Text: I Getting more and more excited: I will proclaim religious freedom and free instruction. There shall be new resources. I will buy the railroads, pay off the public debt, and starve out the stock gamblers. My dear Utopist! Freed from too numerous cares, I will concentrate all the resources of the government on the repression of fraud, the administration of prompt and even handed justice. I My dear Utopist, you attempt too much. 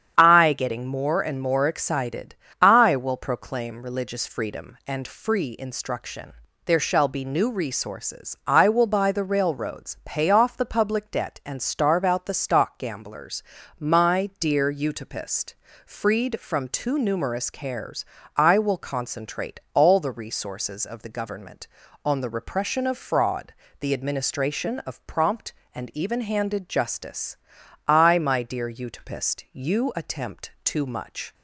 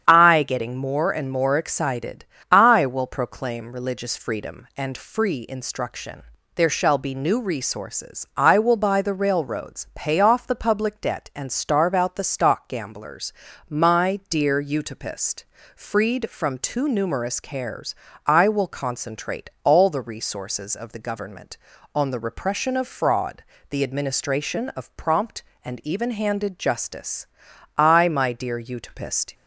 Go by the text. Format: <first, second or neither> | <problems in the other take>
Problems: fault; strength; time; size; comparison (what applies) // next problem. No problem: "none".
first | starts louder than the rest; strong; until 1.0 s; 8.5 dB; strong in the first // stops before "you attempt too much"; at 29.3 s